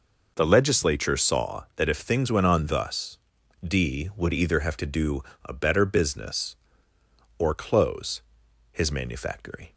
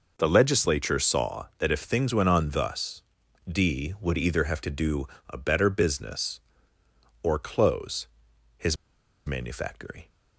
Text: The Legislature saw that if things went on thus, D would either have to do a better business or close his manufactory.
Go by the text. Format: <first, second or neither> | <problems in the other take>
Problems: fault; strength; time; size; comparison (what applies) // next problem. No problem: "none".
first | pauses between "do" and "a"; slight; at 5.0 s; 0.22 s long; slight in the first // pauses between "close" and "his"; noticeable; at 8.0 s; 0.50 s long; noticeable in the first // pauses between "his" and "manufactory"; noticeable; at 8.7 s; 0.52 s long